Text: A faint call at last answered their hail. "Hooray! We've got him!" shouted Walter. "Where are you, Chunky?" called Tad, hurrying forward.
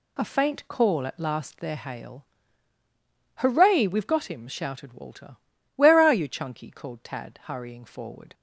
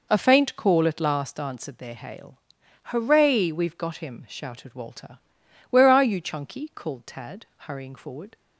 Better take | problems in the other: second | skips "answered"; at 1.5 s

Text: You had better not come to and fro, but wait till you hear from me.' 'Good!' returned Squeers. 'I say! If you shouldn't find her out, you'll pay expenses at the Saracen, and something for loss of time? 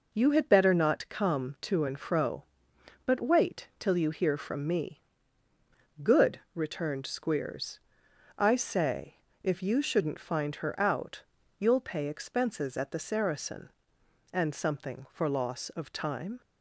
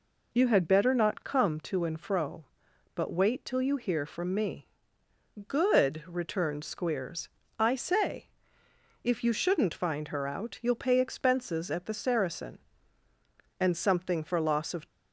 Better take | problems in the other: first | stops before "time"; at 14.8 s

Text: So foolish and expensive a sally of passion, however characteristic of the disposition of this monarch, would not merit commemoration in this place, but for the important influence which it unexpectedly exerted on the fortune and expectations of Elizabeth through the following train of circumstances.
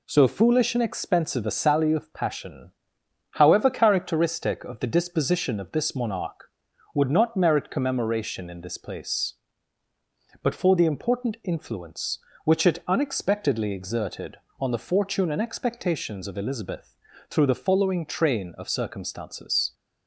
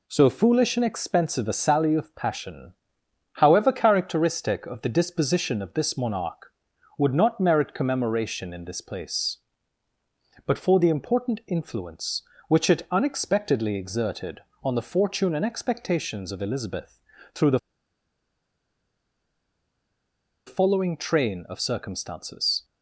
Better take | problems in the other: first | pauses between "Elizabeth" and "through"; slight; at 16.9 s; 0.34 s long; slight in the first // pauses between "the" and "following"; strong; at 17.5 s; 2.8 s long

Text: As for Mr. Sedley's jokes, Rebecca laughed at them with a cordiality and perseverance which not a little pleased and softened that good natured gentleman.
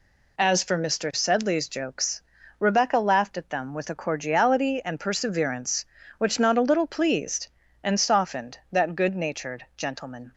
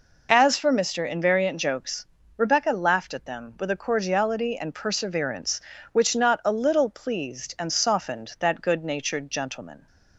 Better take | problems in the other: first | says "Invariant" for "Sedley's"; at 1.0 s

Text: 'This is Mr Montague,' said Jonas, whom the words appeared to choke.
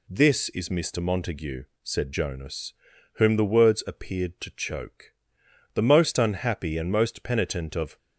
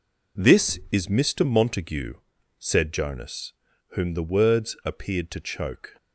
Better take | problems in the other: second | goes on to say "The most unhappy and most penitent of"; strong; from 5.7 s on; 2.2 s long

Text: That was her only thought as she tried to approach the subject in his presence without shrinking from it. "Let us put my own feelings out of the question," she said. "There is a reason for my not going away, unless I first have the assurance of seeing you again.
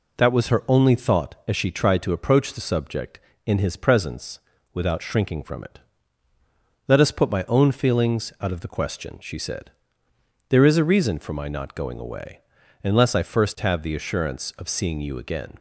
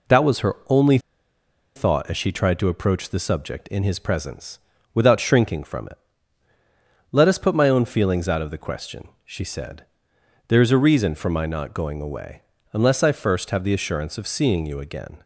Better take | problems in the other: first | pauses between "only" and "thought"; noticeable; at 0.9 s; 0.77 s long // pauses between "presence" and "without"; slight; at 4.5 s; 0.34 s long; slight in the first

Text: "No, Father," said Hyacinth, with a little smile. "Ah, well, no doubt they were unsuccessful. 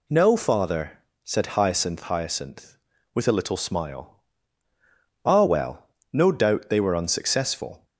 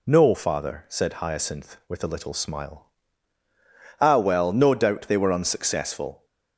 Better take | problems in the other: second | says "Hyacinth" twice; at 2.0 s

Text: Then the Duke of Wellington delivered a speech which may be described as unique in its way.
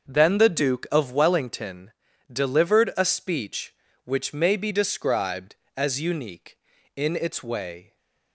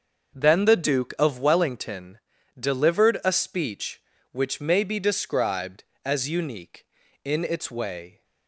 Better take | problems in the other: neither | starts louder than the rest; the same in both // pauses between "Wellington" and "delivered"; the same in both

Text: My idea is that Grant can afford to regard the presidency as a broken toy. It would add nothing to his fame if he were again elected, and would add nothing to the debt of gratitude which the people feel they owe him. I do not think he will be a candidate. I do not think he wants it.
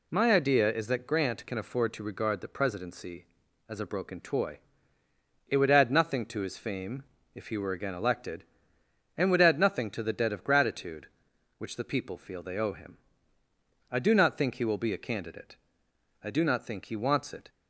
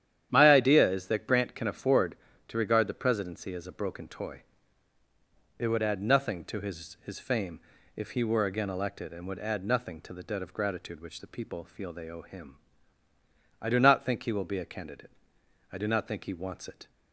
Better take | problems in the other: first | starts louder than the rest; strong; until 1.3 s; 10 dB // says "his" twice; at 7.0 s // pauses between "fame" and "if"; slight; at 7.5 s; 0.36 s long; slight in the first

